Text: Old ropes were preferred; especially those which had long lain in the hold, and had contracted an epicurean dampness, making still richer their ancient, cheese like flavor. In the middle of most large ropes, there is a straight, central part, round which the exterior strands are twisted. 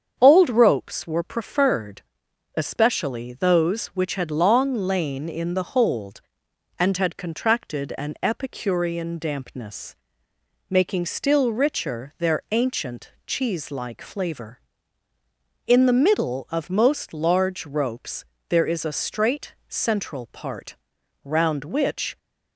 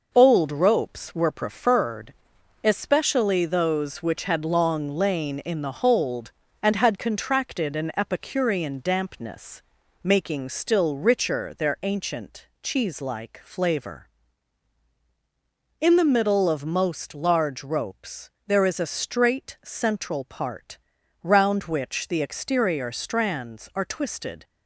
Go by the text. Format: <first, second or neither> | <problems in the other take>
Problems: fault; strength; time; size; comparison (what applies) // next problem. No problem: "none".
second | starts louder than the rest; strong; until 1.2 s; 7.5 dB // stops before "the exterior strands are twisted"; at 22.1 s